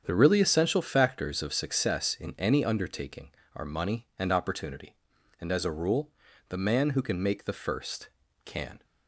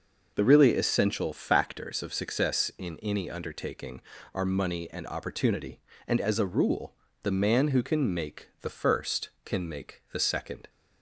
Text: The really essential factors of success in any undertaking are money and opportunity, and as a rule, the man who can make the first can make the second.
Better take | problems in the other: second | starts louder than the rest; strong; until 1.0 s; 8 dB // stops before "make the second"; at 8.8 s

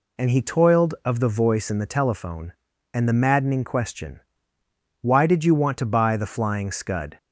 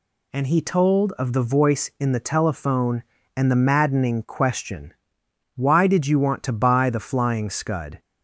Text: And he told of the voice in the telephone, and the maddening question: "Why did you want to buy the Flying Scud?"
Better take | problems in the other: second | says "toiled" for "told"; at 0.4 s

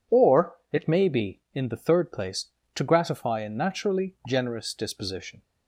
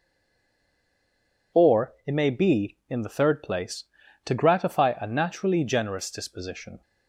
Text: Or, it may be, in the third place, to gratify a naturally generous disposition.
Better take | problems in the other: first | stays silent before the first word; noticeable; until 1.5 s; 1.5 s long

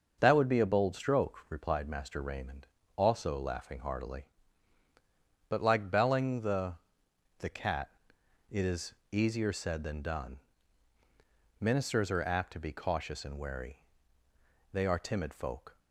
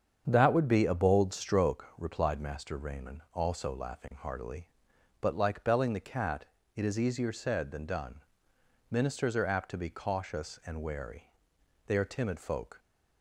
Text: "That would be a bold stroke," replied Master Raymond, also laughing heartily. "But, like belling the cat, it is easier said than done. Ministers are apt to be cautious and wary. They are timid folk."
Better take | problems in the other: second | starts louder than the rest; until 1.2 s; 6 dB; strong in the second // says "the" twice; at 7.3 s // pauses between "is" and "easier"; slight; at 8.9 s; 0.20 s long

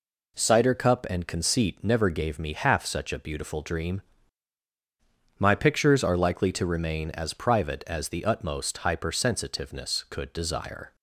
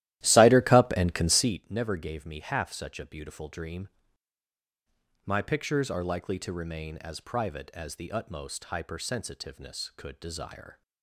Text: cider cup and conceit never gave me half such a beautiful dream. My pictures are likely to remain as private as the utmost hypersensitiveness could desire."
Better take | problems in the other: first | starts louder than the rest; strong; until 1.5 s; 14.5 dB

